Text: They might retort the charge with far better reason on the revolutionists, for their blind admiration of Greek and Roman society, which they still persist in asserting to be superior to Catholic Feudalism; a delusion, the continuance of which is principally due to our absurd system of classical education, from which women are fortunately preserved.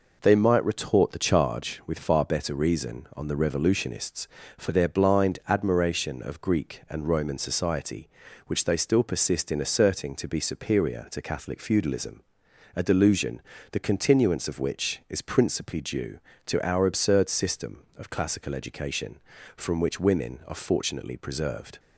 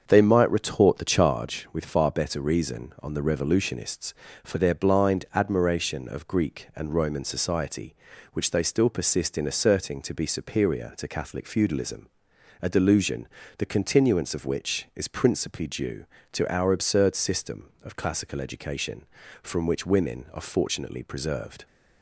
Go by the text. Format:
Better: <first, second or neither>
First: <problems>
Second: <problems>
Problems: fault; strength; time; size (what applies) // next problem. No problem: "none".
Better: first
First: none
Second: starts louder than the rest; until 1.4 s; 7 dB